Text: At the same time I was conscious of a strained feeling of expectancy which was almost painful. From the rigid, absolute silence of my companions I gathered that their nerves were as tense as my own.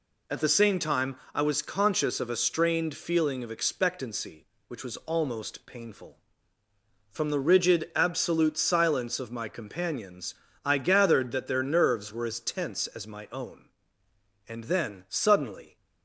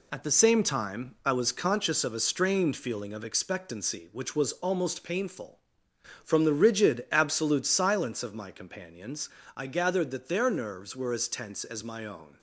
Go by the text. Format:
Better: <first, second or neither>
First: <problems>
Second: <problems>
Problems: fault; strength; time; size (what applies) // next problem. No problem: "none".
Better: second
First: pauses between "time" and "I"; slight; at 1.1 s; 0.18 s long // pauses between "companions" and "I"; slight; at 10.3 s; 0.32 s long // goes on to say "And then suddenly"; noticeable; from 14.4 s on; 1.2 s long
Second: pauses between "companions" and "I"; slight; at 9.2 s; 0.28 s long